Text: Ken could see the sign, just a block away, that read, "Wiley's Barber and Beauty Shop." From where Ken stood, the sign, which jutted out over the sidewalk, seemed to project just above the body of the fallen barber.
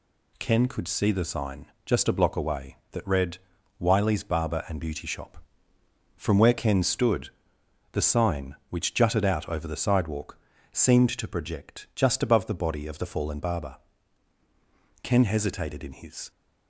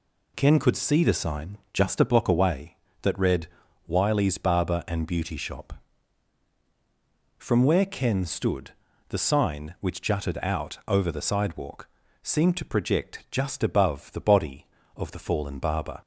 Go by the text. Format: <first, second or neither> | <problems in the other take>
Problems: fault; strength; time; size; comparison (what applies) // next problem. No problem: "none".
second | goes on to say "Ken hesitated in his"; noticeable; from 15.0 s on; 1.2 s long